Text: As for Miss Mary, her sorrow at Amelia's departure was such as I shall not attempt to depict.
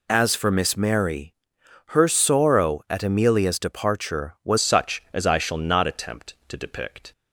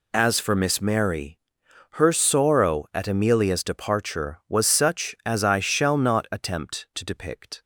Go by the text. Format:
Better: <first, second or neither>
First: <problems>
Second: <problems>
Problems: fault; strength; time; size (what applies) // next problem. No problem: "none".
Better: second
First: changes voice at "such"; from 4.5 s on; 2.6 s long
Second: none